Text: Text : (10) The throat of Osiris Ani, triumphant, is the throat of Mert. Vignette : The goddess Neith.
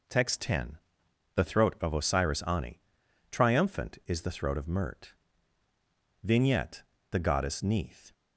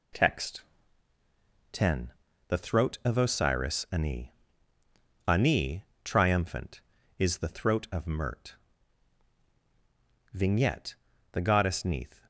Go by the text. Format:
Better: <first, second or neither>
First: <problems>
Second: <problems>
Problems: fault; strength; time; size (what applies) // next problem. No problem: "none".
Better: first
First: none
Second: says "Ani" twice; at 5.2 s